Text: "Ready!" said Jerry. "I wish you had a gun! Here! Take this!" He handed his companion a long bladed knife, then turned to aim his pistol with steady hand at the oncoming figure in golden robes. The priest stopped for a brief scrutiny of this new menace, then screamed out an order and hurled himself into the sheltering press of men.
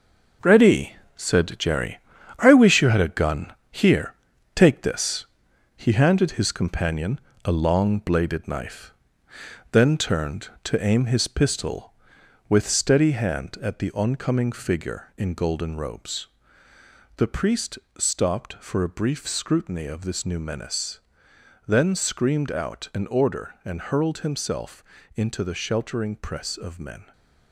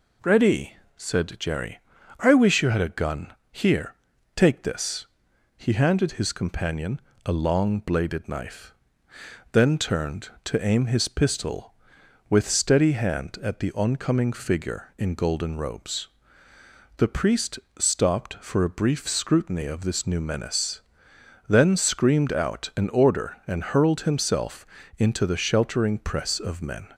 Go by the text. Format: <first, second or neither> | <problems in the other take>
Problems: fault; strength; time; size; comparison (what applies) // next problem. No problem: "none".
second | gets quieter; strong; throughout; 7.5 dB // pauses between "companion" and "a"; slight; at 7.1 s; 0.24 s long; slight in the second // pauses between "priest" and "stopped"; slight; at 17.7 s; 0.20 s long; slight in the second // pauses between "himself" and "into"; slight; at 24.8 s; 0.32 s long; slight in the second